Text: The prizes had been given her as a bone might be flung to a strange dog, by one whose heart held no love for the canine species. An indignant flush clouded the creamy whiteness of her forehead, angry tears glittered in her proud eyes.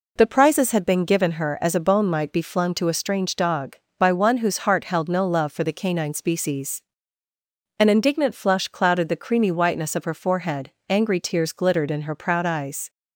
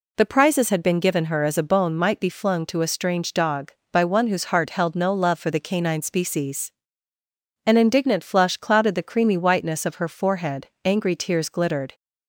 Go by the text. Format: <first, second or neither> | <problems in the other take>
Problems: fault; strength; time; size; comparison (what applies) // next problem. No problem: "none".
first | stops before "in her proud eyes"; at 11.9 s